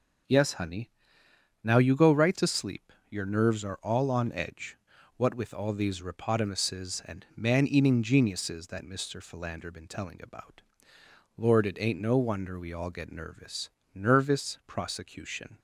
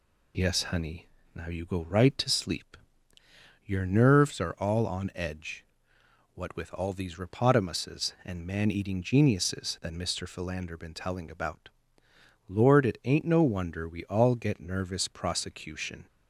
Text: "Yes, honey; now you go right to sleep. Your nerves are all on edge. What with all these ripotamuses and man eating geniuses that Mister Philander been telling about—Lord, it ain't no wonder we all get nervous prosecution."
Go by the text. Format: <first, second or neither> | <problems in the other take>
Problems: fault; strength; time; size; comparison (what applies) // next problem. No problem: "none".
second | says "nervous" twice; at 13.9 s